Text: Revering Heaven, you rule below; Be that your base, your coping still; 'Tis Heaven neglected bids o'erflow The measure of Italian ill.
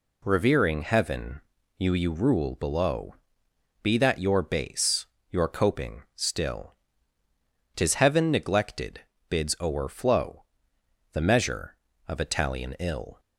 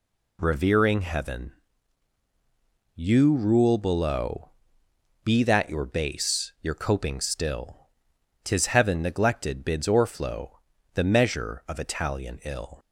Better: second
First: says "you" twice; at 1.9 s // pauses between "neglected" and "bids"; slight; at 9.0 s; 0.26 s long // pauses between "o'erflow" and "The"; noticeable; at 10.4 s; 0.66 s long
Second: pauses between "o'erflow" and "The"; slight; at 10.5 s; 0.34 s long

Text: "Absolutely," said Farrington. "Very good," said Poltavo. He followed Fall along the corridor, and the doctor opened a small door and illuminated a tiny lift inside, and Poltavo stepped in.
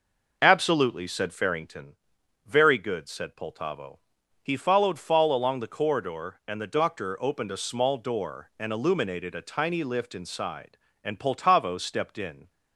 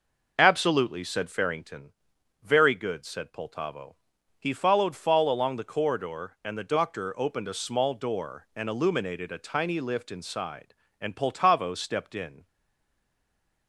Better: first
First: none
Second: stays silent after the last word; noticeable; from 12.4 s on; 1.2 s long

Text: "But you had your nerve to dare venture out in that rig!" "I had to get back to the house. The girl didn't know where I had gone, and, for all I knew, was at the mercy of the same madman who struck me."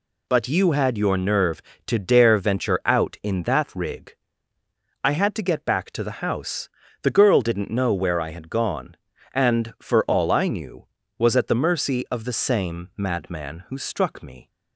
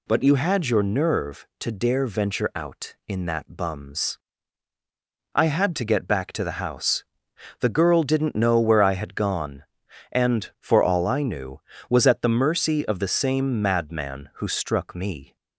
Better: first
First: none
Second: says "bums" for "rig"; at 3.5 s

